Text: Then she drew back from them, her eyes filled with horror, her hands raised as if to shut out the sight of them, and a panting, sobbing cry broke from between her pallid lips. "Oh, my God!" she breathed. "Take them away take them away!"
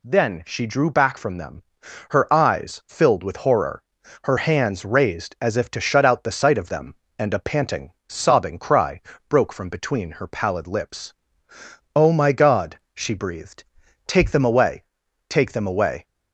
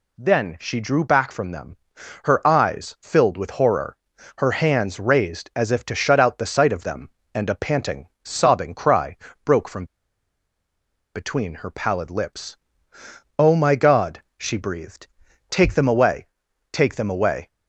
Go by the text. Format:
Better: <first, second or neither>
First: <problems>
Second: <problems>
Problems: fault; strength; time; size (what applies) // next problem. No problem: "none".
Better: first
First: pauses between "cry" and "broke"; slight; at 8.9 s; 0.30 s long // pauses between "away" and "take"; noticeable; at 14.8 s; 0.46 s long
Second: pauses between "cry" and "broke"; slight; at 9.1 s; 0.30 s long // pauses between "from" and "between"; strong; at 9.8 s; 1.2 s long // pauses between "away" and "take"; noticeable; at 16.2 s; 0.46 s long